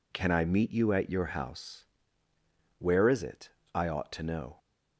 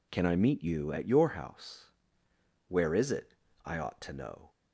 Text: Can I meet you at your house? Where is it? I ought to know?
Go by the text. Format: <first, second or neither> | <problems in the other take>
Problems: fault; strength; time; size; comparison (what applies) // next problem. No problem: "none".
neither | none